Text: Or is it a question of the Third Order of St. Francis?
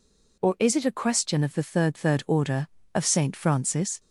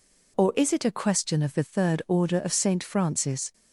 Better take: second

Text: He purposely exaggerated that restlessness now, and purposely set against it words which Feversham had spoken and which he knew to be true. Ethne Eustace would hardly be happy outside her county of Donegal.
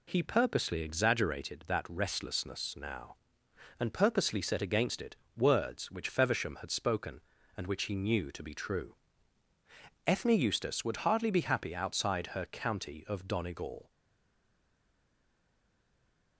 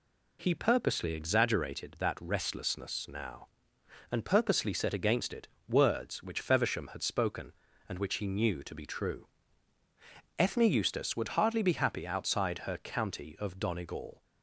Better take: second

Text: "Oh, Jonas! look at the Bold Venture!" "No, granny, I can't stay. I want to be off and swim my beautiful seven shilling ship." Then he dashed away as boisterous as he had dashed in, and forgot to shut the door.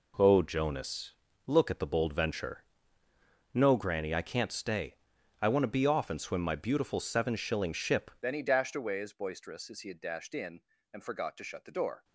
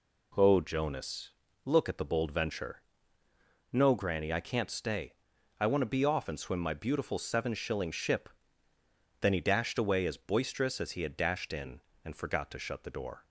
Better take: second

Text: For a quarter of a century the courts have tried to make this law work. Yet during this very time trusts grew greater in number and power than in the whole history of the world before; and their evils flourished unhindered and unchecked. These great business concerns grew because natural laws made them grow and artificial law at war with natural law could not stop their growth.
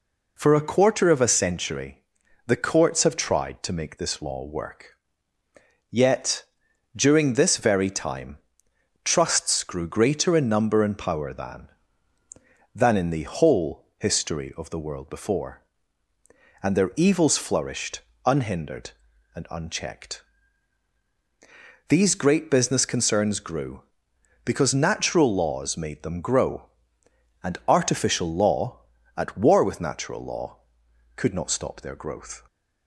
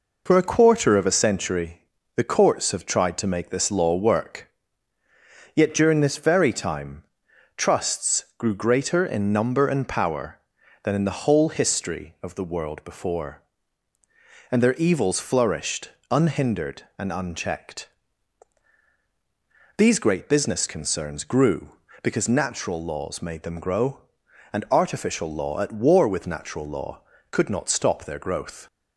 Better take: second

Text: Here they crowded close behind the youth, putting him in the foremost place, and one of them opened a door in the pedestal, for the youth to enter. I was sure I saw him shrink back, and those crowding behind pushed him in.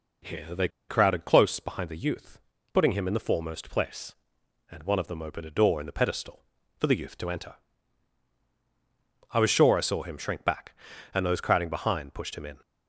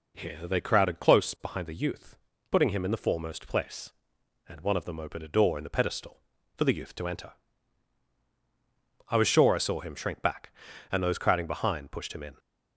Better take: second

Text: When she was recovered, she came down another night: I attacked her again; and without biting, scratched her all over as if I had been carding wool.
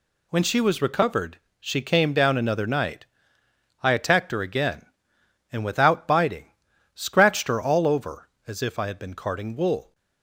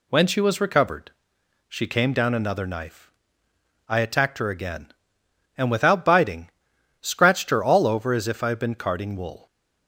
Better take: first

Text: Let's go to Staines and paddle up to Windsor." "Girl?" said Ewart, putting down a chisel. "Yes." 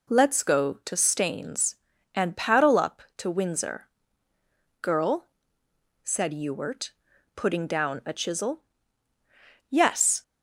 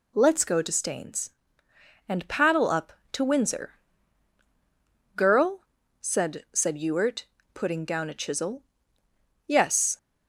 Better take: first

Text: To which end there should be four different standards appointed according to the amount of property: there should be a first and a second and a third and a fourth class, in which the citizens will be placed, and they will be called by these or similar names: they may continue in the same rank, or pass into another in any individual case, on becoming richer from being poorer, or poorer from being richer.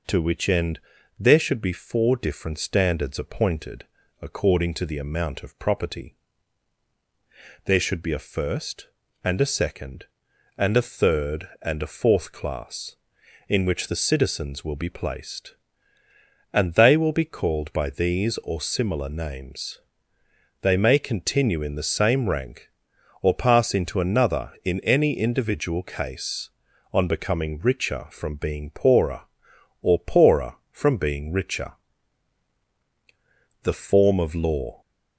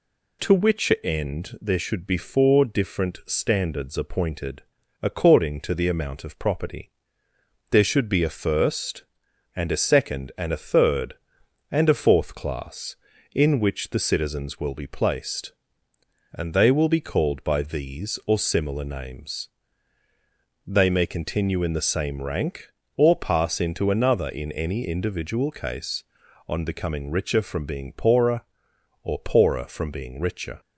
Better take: second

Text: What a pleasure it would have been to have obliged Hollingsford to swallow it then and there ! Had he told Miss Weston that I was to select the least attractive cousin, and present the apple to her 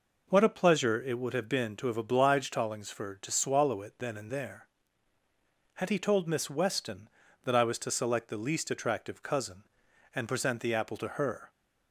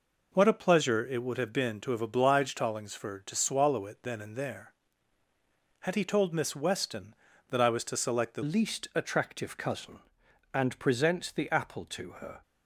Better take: first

